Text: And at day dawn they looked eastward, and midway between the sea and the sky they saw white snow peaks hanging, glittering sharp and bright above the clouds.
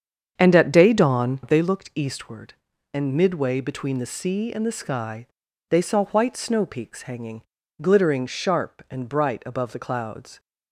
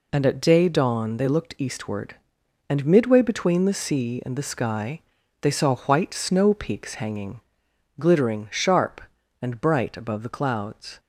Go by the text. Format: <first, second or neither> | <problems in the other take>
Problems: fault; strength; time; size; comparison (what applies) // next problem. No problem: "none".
second | starts louder than the rest; strong; until 1.7 s; 7.5 dB // pauses between "sky" and "they"; at 5.2 s; 0.42 s long; also in the second